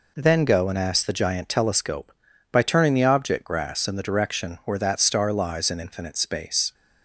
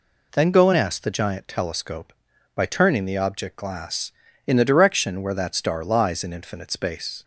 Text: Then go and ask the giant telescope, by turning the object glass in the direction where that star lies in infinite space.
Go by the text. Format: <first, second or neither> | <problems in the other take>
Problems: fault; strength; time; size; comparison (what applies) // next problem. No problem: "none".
second | says "grass" for "glass"; at 3.4 s